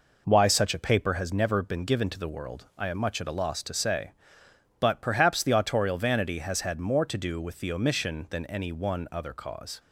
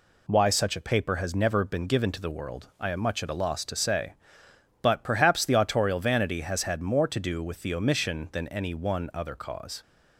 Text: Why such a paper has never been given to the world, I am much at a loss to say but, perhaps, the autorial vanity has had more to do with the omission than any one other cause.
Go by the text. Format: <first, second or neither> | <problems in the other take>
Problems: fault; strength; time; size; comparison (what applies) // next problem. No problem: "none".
second | starts louder than the rest; noticeable; until 1.3 s; 4.5 dB